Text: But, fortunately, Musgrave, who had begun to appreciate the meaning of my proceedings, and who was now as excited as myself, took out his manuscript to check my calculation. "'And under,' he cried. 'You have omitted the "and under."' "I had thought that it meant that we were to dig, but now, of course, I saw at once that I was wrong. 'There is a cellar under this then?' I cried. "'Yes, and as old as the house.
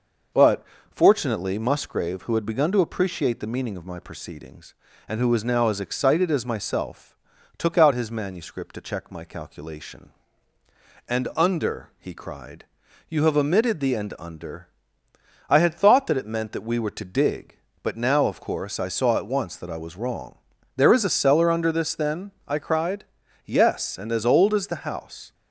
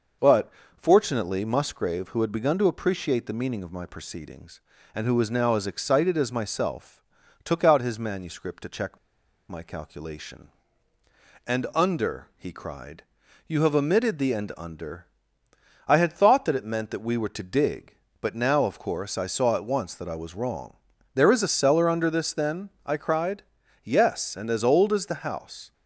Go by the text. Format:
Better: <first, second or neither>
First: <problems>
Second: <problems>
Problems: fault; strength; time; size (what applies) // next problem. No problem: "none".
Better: first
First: none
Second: pauses between "check" and "my"; noticeable; at 8.9 s; 0.52 s long